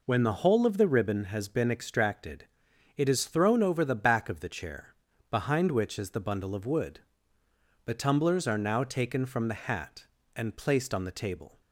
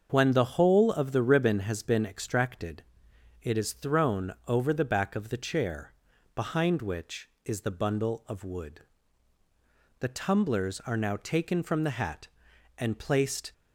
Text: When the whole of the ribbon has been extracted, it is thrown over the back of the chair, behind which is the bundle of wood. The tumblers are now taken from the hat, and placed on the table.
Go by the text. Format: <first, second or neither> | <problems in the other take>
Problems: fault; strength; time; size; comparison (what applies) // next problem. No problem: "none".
first | starts louder than the rest; until 1.1 s; 6.5 dB // stops before "on the table"; at 13.5 s